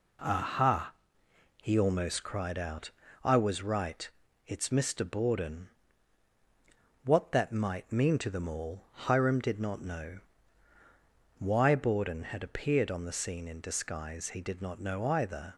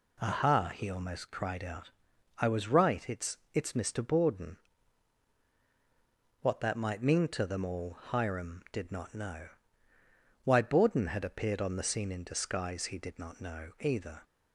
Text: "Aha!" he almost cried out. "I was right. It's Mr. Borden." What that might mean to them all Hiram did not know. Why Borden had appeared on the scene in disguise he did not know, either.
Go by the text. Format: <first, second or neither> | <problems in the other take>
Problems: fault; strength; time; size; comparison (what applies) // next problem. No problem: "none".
first | says "It's" twice; at 3.5 s